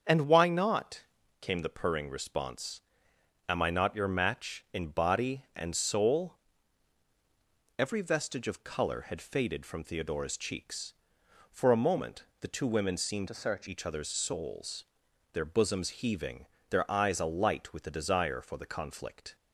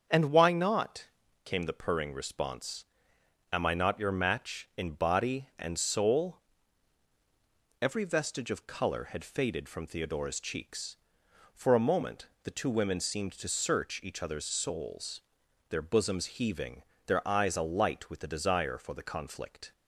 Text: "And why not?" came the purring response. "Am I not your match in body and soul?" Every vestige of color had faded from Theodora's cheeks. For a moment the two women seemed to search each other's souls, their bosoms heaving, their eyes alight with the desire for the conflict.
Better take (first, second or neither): second